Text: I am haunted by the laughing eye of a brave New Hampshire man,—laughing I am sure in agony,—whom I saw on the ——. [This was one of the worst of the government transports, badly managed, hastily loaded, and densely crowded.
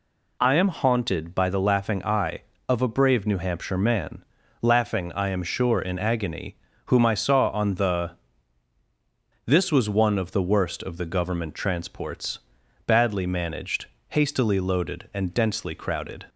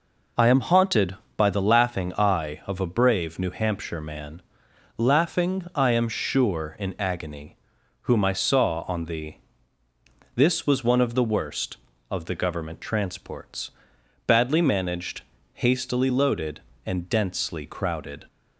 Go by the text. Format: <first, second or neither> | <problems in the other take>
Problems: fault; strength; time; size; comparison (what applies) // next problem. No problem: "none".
neither | none